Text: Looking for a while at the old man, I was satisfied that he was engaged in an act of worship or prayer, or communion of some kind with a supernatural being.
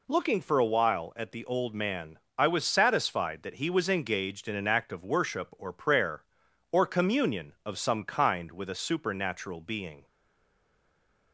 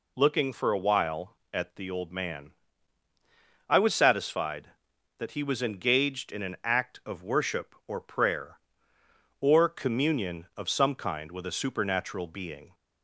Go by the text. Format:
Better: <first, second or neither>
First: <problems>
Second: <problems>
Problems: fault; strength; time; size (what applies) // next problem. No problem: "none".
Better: second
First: stays silent after the last word; noticeable; from 10.0 s on; 1.3 s long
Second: none